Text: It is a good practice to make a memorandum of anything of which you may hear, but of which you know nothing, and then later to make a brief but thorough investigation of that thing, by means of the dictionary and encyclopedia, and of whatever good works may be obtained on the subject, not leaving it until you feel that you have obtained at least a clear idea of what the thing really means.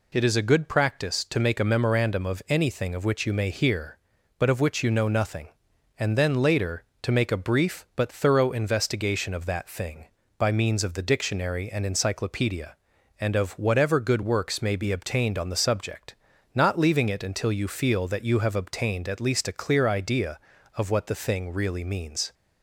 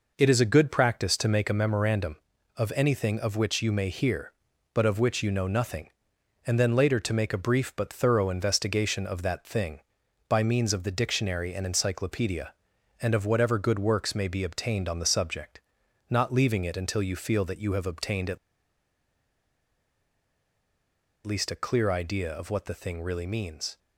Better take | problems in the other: first | pauses between "at" and "least"; strong; at 18.3 s; 2.8 s long

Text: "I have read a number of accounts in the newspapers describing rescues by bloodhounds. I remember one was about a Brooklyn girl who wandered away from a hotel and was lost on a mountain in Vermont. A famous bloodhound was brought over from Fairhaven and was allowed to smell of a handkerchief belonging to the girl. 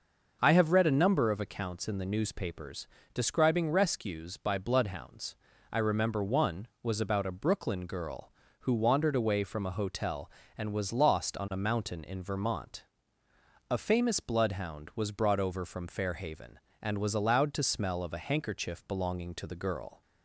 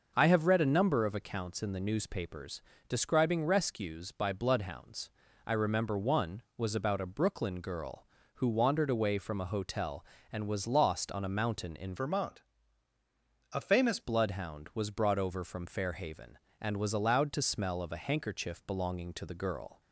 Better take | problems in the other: first | pauses between "newspapers" and "describing"; slight; at 2.6 s; 0.26 s long; slight in the first // changes voice from "Vermont" to "famous"; from 11.9 to 13.9 s; 2.0 s long

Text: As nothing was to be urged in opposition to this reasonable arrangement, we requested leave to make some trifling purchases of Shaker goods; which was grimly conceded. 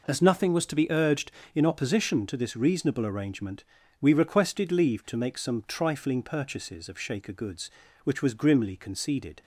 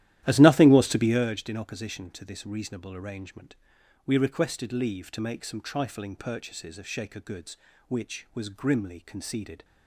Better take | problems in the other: first | starts louder than the rest; strong; until 1.3 s; 13.5 dB

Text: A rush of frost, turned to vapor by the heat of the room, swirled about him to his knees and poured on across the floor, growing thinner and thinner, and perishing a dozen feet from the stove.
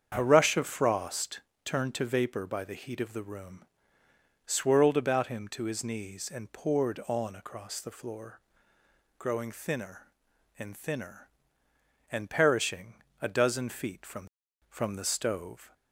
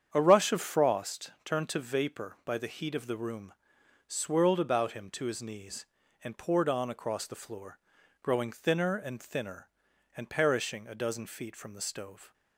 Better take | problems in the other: second | starts louder than the rest; strong; until 1.1 s; 7.5 dB; strong in the second // pauses between "perishing" and "a"; slight; at 12.9 s; 0.30 s long // says "from" twice; at 14.6 s

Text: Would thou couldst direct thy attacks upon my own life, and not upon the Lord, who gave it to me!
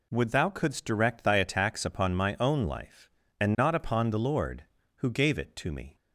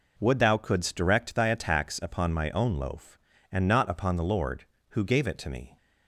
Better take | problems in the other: first | says "loaf" for "life"; at 2.7 s

